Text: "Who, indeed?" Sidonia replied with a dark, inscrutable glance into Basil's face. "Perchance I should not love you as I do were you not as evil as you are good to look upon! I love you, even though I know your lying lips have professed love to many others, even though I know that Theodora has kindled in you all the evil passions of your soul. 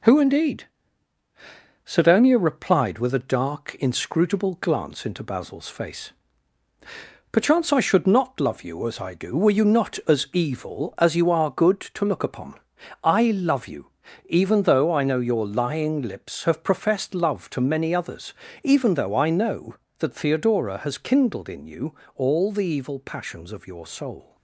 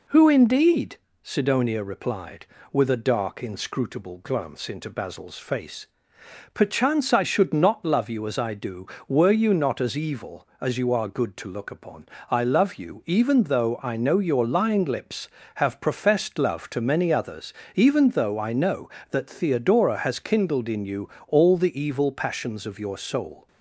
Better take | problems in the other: second | gets quieter; noticeable; throughout; 4.5 dB // pauses between "you" and "all"; slight; at 21.9 s; 0.22 s long; slight in the second

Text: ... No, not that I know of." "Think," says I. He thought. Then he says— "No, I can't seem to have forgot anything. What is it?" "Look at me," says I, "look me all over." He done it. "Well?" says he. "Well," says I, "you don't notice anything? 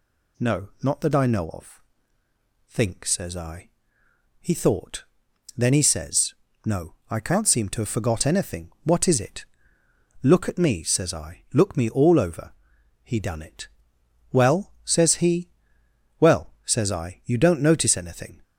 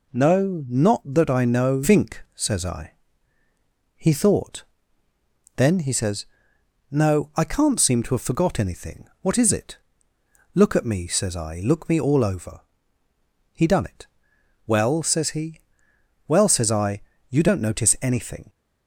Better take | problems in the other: first | skips "of"; at 1.8 s

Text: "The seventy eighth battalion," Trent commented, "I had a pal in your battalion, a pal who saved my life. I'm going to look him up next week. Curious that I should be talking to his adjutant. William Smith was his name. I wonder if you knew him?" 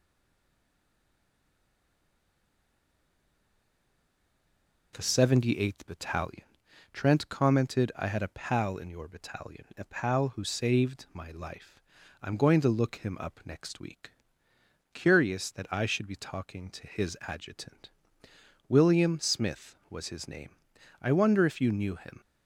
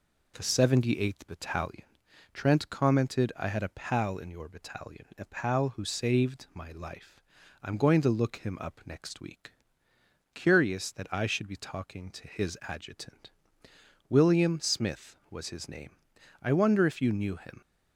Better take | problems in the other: second | stays silent before the first word; strong; until 4.9 s; 4.9 s long

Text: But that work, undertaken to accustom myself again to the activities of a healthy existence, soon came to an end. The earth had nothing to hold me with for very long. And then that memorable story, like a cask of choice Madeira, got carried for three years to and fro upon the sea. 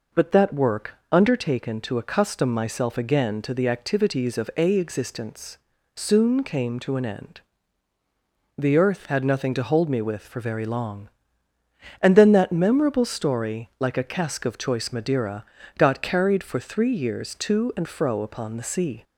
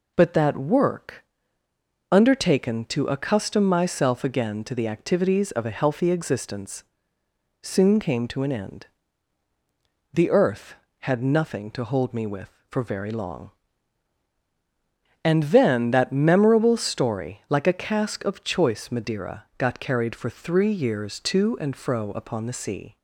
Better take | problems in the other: second | skips "healthy"; at 4.7 s

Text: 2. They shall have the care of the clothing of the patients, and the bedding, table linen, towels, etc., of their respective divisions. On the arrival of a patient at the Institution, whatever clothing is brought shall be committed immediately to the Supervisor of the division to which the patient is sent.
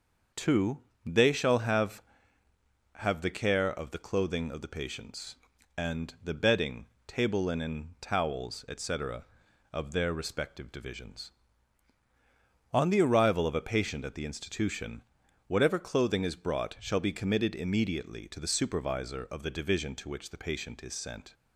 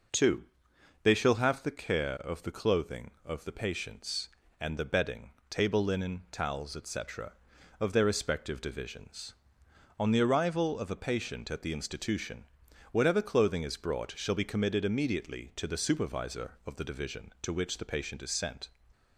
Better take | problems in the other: second | starts louder than the rest; noticeable; until 1.5 s; 6 dB // says "have" twice; at 2.9 s

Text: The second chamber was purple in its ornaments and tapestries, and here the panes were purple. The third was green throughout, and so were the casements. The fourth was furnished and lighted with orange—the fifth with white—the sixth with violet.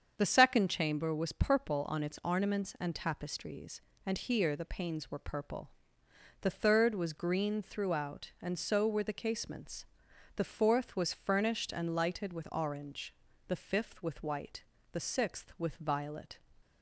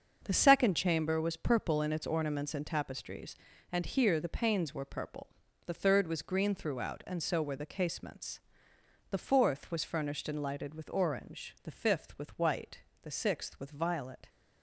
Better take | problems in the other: second | starts louder than the rest; strong; until 1.1 s; 7 dB; also in the second // says "on" for "in"; at 1.8 s

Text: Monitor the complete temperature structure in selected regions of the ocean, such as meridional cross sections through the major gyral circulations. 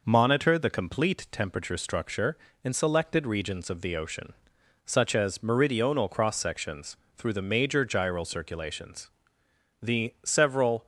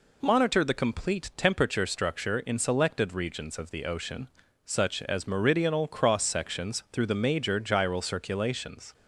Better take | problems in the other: second | pauses between "sections" and "through"; slight; at 6.9 s; 0.18 s long // goes on to say "The several"; noticeable; from 9.8 s on; 1.0 s long

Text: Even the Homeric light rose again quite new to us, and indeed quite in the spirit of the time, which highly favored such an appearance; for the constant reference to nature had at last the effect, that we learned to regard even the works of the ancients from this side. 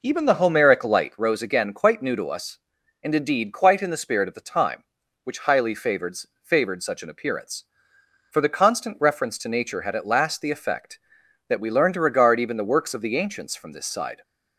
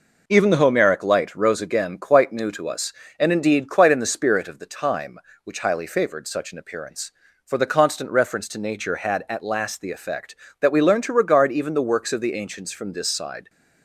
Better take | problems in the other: second | says "favored" twice; at 6.4 s

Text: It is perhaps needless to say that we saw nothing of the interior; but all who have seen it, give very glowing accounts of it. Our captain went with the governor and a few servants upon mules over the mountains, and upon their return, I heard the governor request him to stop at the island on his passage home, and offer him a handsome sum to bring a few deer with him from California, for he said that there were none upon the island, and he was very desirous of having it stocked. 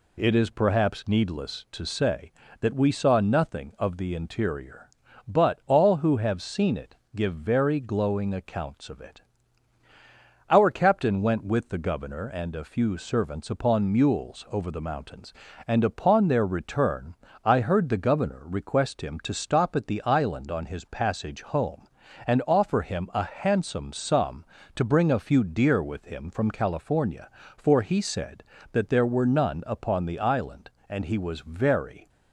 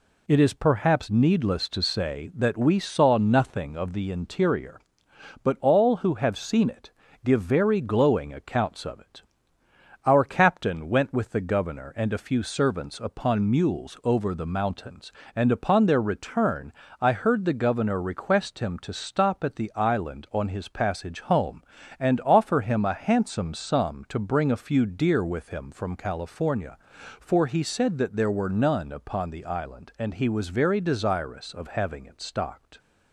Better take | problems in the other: second | stops before "desirous of having it stocked"; at 32.0 s

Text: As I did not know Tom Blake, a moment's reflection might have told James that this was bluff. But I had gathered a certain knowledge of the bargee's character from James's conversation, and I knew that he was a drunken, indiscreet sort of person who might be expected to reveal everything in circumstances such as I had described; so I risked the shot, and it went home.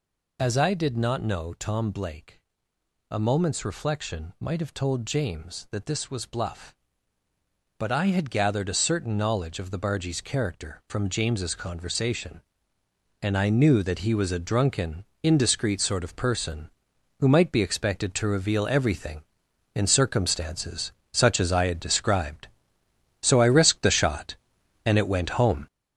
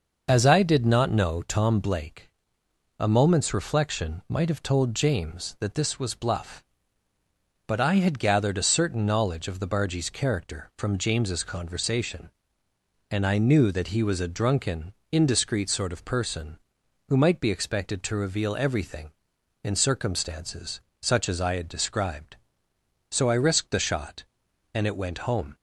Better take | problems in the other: second | gets louder; throughout; 6.5 dB // pauses between "circumstances" and "such"; slight; at 20.9 s; 0.22 s long; slight in the second

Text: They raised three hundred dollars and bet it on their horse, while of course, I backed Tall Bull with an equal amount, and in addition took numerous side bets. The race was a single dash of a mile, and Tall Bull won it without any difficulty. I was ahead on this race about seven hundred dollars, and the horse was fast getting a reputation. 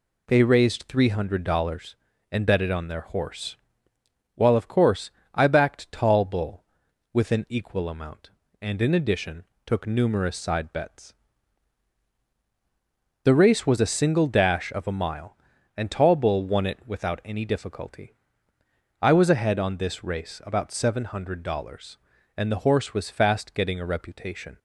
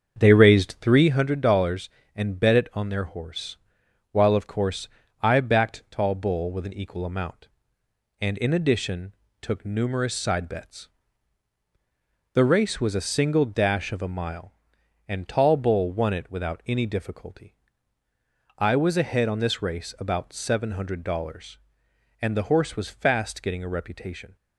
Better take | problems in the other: first | starts louder than the rest; until 1.1 s; 7 dB // pauses between "addition" and "took"; slight; at 9.1 s; 0.28 s long; slight in the first

